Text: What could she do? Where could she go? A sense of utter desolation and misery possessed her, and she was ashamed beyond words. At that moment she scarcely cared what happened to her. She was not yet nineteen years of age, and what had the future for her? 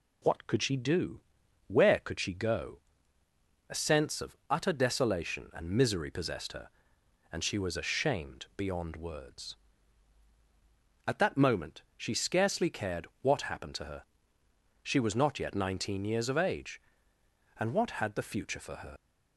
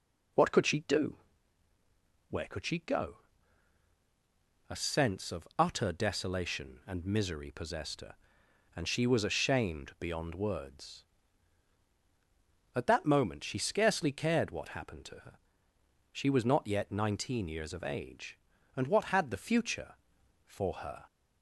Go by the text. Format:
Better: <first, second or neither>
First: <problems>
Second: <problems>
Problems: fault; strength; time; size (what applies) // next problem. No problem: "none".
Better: second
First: pauses between "moment" and "she"; slight; at 11.8 s; 0.16 s long // leaves "her" unfinished; at 18.9 s; 115 ms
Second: none